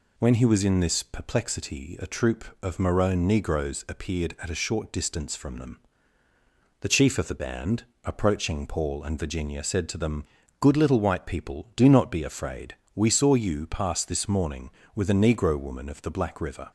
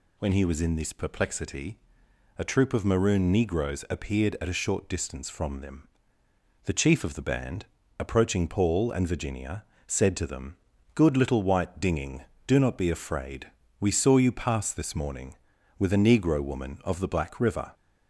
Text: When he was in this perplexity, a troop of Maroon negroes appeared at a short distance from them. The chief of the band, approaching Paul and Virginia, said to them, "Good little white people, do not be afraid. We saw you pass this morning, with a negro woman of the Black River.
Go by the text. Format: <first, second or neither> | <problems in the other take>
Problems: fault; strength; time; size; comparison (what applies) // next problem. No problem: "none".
first | says "dinging" for "people"; at 11.8 s